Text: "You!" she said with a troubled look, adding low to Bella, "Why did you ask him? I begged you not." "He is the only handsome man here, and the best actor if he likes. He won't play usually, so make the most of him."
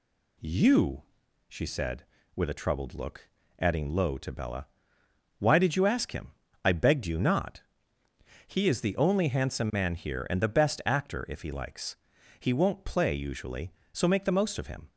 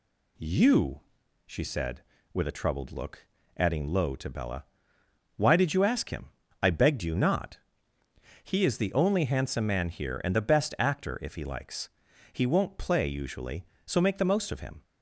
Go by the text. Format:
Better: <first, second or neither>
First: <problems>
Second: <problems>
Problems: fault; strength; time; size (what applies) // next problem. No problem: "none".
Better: neither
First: none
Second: none